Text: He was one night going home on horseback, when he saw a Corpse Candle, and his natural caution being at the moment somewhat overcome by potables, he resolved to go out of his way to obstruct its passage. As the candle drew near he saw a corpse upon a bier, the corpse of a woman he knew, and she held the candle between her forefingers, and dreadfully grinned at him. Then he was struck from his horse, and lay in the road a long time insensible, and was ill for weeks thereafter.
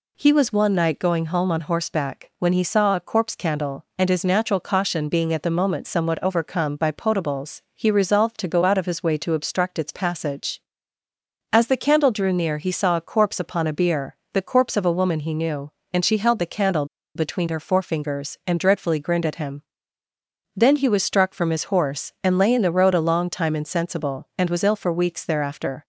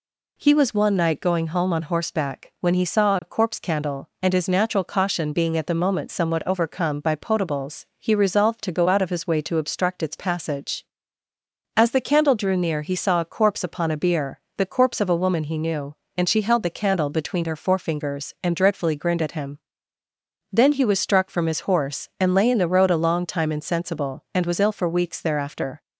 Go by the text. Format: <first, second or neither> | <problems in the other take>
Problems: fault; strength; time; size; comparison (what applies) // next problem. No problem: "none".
second | pauses between "candle" and "between"; slight; at 16.8 s; 0.30 s long